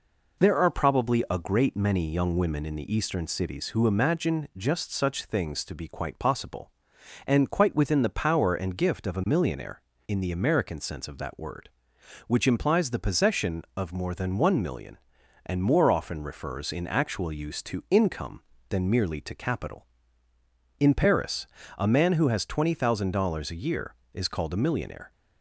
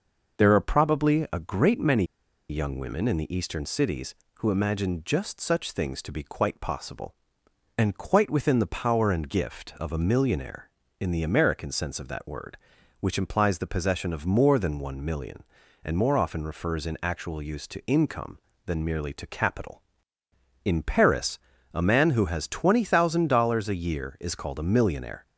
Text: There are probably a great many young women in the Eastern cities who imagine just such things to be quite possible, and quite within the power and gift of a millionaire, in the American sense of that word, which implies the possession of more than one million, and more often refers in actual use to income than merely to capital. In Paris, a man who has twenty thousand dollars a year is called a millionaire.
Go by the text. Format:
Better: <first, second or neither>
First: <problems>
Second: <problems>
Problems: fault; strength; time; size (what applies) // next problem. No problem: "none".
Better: first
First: none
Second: pauses between "many" and "young"; at 2.0 s; 0.45 s long